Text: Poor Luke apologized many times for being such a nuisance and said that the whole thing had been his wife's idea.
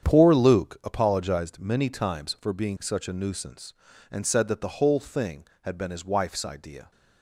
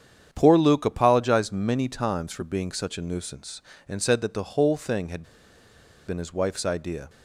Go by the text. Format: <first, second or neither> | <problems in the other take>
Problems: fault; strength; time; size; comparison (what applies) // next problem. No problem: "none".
first | starts louder than the rest; strong; until 1.3 s; 8.5 dB; strong in the first // pauses between "had" and "been"; noticeable; at 5.2 s; 0.84 s long